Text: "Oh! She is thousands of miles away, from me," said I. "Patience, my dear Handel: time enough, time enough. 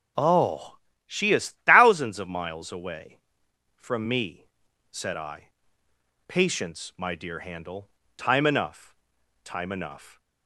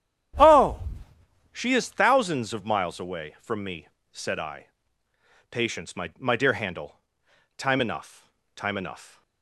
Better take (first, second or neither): first